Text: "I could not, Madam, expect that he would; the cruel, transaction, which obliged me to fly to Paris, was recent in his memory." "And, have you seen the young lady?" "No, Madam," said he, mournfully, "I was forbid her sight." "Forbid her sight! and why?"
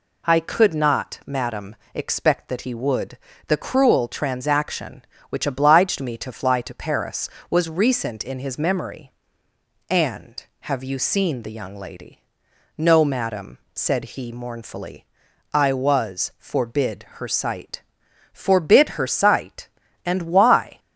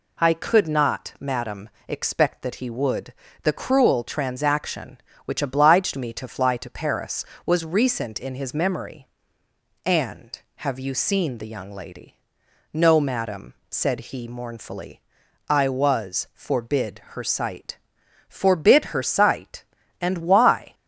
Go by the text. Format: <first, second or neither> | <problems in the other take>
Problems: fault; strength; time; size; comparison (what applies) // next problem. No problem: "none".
neither | none